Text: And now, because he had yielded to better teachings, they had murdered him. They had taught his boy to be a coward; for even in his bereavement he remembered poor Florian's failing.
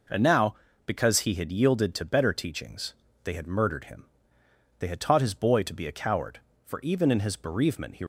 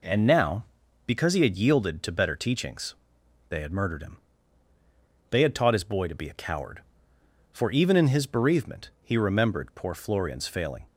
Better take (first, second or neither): second